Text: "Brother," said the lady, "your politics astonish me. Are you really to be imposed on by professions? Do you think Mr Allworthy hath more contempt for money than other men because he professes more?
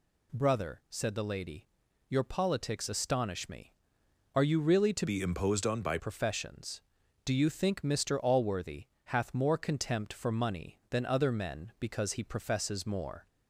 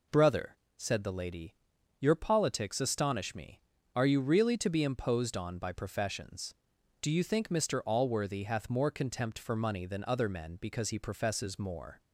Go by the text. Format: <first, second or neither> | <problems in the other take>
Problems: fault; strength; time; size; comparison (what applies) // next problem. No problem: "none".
second | changes voice from "be" to "by"; from 5.0 to 5.9 s; 0.9 s long // pauses between "Allworthy" and "hath"; slight; at 8.8 s; 0.18 s long